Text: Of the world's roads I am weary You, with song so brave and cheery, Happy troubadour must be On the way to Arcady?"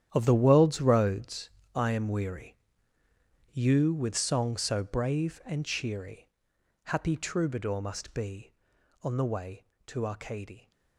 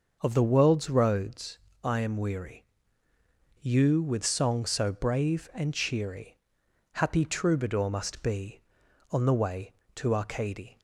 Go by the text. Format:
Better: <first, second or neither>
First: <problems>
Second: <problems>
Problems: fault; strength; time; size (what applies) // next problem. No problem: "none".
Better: second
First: gets quieter; strong; throughout; 14 dB // starts louder than the rest; strong; until 1.1 s; 10 dB // pauses between "roads" and "I"; slight; at 1.5 s; 0.24 s long // pauses between "weary" and "You"; noticeable; at 2.5 s; 0.96 s long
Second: starts louder than the rest; noticeable; until 1.2 s; 6 dB // pauses between "roads" and "I"; slight; at 1.5 s; 0.24 s long // pauses between "weary" and "You"; noticeable; at 2.6 s; 0.96 s long